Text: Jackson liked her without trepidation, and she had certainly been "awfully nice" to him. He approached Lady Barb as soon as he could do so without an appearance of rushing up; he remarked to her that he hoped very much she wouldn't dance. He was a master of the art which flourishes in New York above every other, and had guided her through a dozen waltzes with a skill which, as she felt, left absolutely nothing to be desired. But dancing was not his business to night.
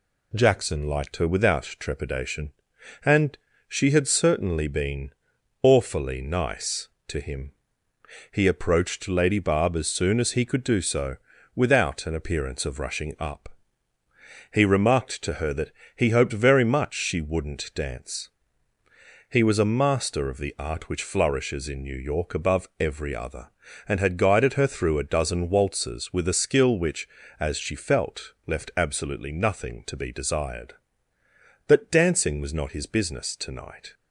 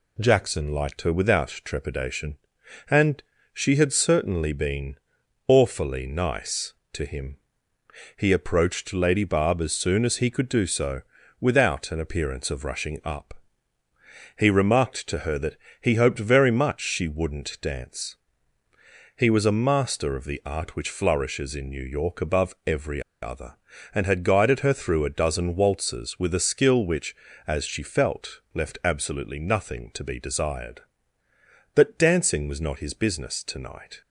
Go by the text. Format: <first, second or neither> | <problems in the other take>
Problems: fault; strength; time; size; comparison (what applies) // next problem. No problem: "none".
first | pauses between "and" and "she"; slight; at 3.2 s; 0.32 s long; slight in the first // pauses between "been" and "awfully"; noticeable; at 4.9 s; 0.52 s long; noticeable in the first // pauses between "so" and "without"; at 11.0 s; 0.38 s long; also in the first // pauses between "that" and "he"; slight; at 15.5 s; 0.26 s long; slight in the first // pauses between "every" and "other"; slight; at 23.0 s; 0.20 s long